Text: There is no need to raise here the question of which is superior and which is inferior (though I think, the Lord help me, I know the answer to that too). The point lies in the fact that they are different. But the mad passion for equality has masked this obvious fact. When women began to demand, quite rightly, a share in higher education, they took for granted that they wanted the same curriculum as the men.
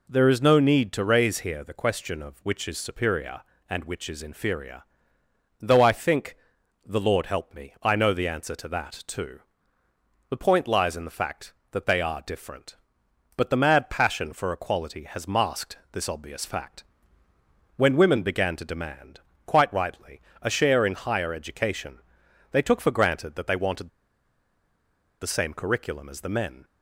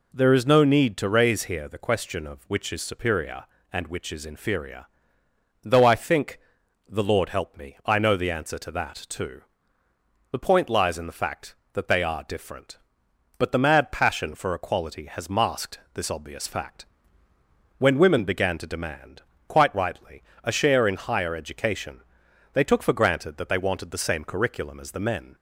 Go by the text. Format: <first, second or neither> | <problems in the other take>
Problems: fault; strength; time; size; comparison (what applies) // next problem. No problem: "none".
second | pauses between "wanted" and "the"; strong; at 23.8 s; 1.3 s long